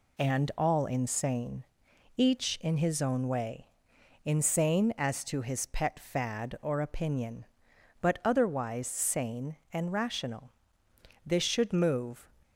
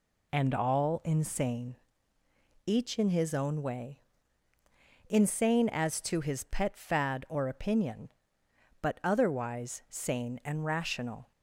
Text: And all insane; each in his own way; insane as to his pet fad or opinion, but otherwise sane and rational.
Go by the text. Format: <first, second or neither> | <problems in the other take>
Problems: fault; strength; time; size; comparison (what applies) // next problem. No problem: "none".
second | goes on to say "This should move"; noticeable; from 11.2 s on; 1.0 s long